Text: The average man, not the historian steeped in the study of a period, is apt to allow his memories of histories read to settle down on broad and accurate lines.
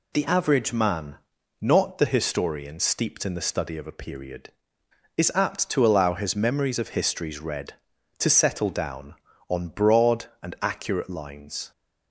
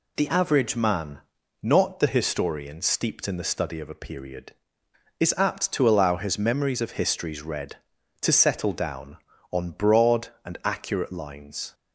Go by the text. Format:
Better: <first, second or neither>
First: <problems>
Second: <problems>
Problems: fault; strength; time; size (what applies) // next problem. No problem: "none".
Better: neither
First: none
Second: none